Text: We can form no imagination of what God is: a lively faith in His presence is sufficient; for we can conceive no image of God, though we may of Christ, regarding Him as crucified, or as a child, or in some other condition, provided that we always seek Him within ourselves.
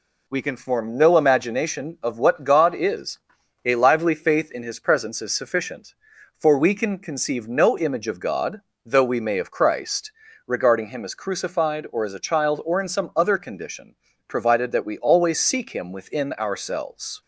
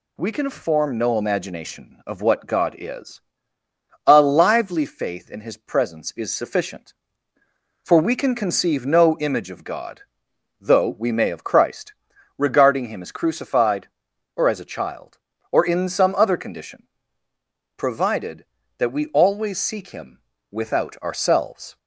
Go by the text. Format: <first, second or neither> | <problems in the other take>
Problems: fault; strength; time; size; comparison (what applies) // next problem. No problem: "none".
first | says "without" for "within"; at 20.4 s